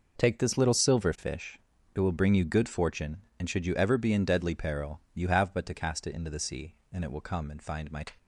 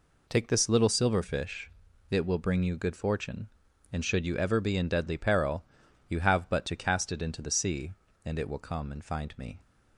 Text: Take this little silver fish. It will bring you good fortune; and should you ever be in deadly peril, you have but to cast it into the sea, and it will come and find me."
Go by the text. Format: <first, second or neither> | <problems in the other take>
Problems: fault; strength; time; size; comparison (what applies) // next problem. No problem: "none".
second | says "my" for "me"; at 7.8 s